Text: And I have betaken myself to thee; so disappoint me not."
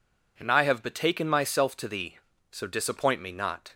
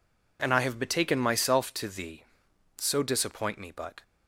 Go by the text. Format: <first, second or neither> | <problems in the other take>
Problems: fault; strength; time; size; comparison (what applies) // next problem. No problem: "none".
first | says "but" for "not"; at 3.7 s